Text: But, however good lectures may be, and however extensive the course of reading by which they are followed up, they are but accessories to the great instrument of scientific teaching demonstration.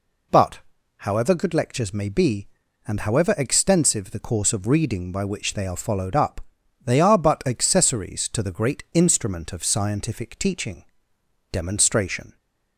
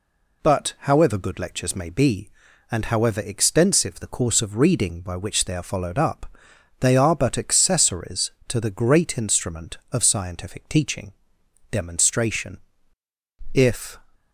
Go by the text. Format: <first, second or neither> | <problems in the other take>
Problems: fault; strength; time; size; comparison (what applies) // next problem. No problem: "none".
first | pauses between "teaching" and "demonstration"; noticeable; at 11.1 s; 0.58 s long; noticeable in the first // goes on to say "If"; slight; from 13.5 s on; 0.44 s long